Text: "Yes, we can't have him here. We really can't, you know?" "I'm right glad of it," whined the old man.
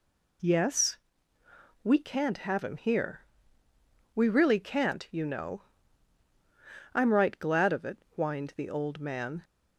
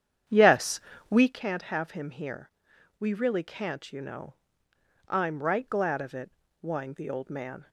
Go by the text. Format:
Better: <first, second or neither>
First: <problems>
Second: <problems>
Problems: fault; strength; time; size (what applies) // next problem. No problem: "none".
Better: first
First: none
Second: starts louder than the rest; strong; until 1.3 s; 9 dB